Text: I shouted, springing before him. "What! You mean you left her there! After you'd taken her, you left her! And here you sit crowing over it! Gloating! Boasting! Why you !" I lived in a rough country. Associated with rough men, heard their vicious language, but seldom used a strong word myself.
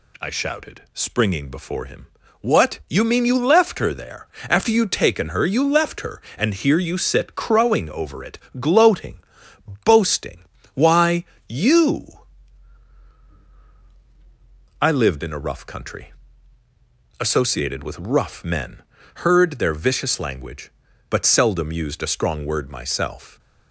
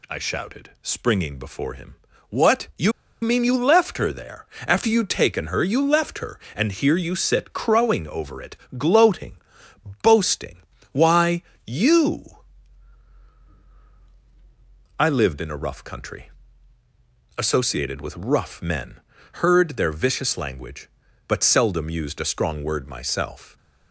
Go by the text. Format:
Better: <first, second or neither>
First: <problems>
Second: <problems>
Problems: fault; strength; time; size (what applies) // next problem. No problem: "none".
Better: first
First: pauses between "Why" and "you"; slight; at 11.2 s; 0.24 s long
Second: pauses between "You" and "mean"; slight; at 2.9 s; 0.30 s long // pauses between "Why" and "you"; slight; at 11.4 s; 0.24 s long